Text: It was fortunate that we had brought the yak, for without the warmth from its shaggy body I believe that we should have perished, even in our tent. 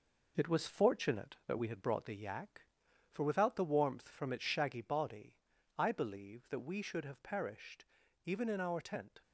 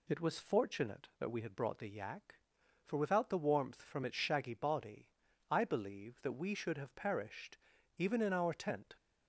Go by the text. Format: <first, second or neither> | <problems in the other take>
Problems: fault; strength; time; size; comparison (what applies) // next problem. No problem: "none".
second | gets quieter; noticeable; throughout; 5 dB // pauses between "body" and "I"; at 5.3 s; 0.42 s long; also in the second